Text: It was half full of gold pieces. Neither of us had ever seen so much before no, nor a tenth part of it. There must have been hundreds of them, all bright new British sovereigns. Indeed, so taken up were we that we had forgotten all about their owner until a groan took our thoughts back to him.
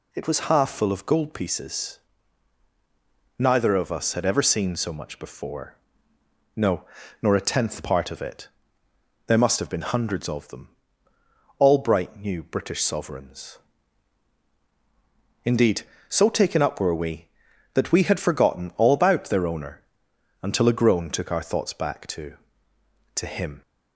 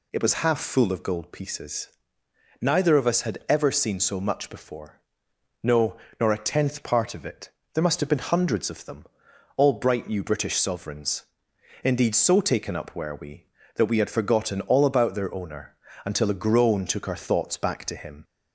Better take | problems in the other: second | pauses between "before" and "no"; noticeable; at 5.7 s; 0.78 s long; noticeable in the second // pauses between "owner" and "until"; noticeable; at 19.8 s; 0.60 s long; slight in the second // says "to" twice; at 23.1 s

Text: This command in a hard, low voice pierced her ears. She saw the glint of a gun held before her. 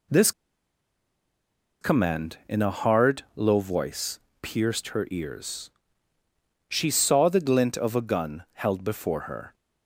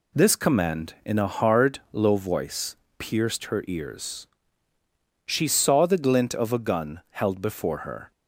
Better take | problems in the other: second | pauses between "This" and "command"; strong; at 0.3 s; 1.5 s long // pauses between "voice" and "pierced"; slight; at 4.1 s; 0.24 s long; slight in the second

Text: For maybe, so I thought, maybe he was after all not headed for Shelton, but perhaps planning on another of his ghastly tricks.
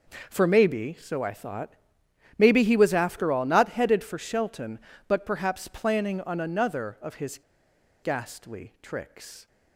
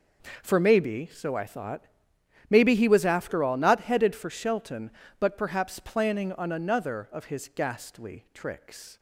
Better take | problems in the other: second | pauses between "his" and "ghastly"; noticeable; at 7.3 s; 0.64 s long

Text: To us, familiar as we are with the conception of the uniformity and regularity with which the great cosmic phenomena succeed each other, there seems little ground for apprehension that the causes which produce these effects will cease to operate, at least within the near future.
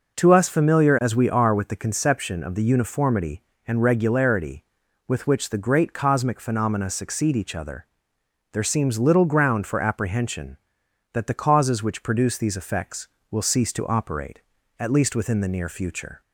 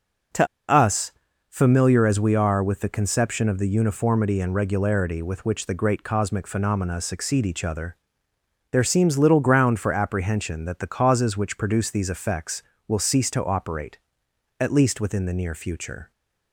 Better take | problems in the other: first | pauses between "To" and "us"; slight; at 0.4 s; 0.23 s long

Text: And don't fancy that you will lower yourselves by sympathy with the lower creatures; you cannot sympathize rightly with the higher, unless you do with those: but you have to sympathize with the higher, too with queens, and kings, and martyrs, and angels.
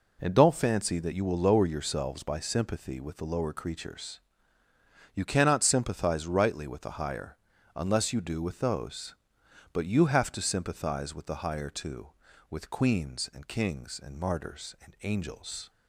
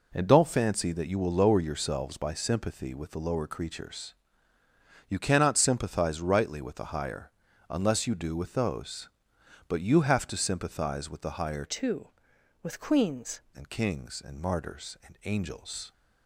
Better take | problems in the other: first | changes voice from "too" to "queens"; from 11.6 to 13.3 s; 1.7 s long

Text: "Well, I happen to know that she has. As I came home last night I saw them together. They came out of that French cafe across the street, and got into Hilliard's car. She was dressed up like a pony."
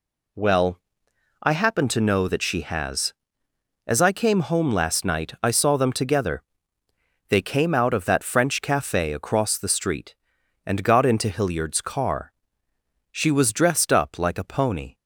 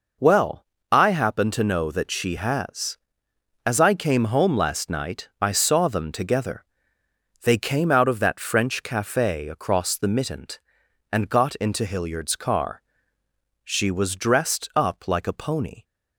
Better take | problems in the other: first | says "mittent" for "street"; at 10.0 s

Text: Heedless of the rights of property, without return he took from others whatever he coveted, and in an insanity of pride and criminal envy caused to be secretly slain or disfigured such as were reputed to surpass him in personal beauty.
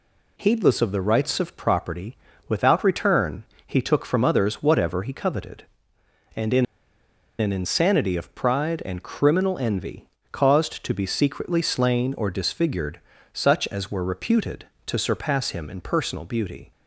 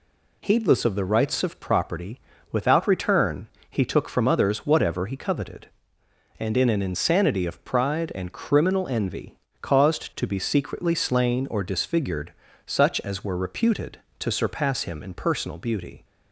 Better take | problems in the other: second | pauses between "return" and "he"; slight; at 3.4 s; 0.22 s long; slight in the second // pauses between "in" and "an"; noticeable; at 6.6 s; 0.75 s long // pauses between "envy" and "caused"; slight; at 10.0 s; 0.24 s long; slight in the second // pauses between "disfigured" and "such"; slight; at 13.0 s; 0.32 s long; slight in the second

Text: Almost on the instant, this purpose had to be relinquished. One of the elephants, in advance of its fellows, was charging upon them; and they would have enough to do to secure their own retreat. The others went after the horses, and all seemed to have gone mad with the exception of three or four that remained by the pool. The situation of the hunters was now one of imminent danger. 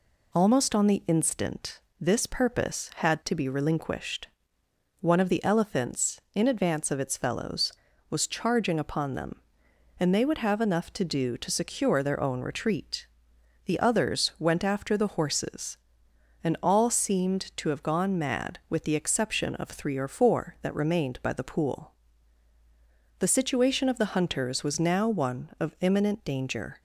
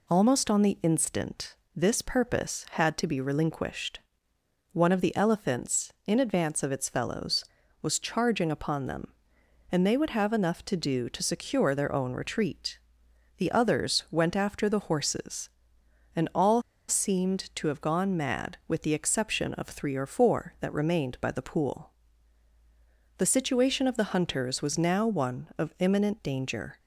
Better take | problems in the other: first | pauses between "all" and "seemed"; slight; at 16.6 s; 0.27 s long

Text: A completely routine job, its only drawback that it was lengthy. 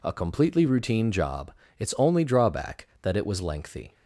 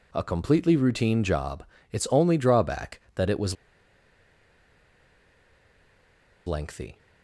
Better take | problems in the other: first | pauses between "was" and "lengthy"; strong; at 3.5 s; 2.9 s long

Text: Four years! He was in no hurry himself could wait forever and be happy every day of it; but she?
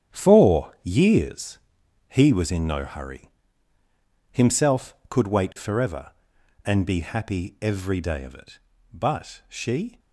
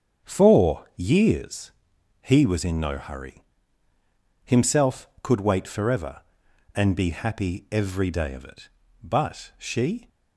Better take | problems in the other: second | gets quieter; strong; throughout; 10.5 dB // starts louder than the rest; strong; until 1.2 s; 9.5 dB; strong in the second // pauses between "hurry" and "himself"; at 3.2 s; 1.0 s long; also in the second

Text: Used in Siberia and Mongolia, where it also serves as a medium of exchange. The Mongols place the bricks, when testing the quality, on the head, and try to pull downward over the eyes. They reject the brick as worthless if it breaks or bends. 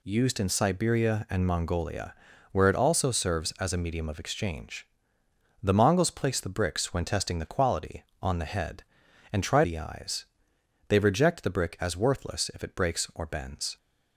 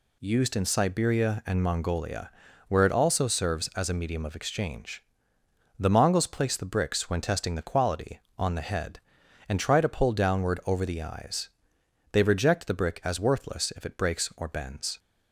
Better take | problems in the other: second | skips "to pull downward over"; at 9.6 s

